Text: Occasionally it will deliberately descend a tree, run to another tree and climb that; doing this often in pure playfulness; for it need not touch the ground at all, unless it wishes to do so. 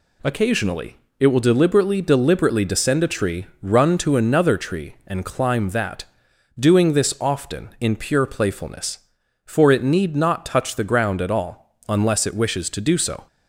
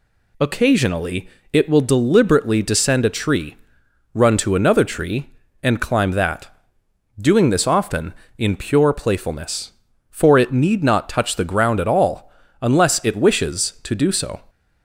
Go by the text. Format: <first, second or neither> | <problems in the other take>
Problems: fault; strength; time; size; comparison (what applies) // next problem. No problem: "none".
second | pauses between "Occasionally" and "it"; slight; at 0.9 s; 0.22 s long; slight in the second // says "deliberately" twice; at 2.0 s